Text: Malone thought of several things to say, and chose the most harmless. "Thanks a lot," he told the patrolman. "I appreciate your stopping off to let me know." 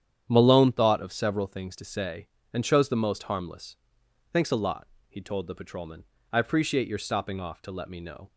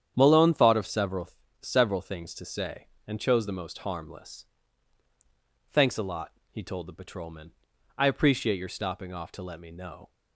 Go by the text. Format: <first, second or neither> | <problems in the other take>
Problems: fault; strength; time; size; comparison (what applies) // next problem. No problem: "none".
first | starts louder than the rest; strong; until 1.1 s; 9 dB; strong in the first // says "several" twice; at 1.6 s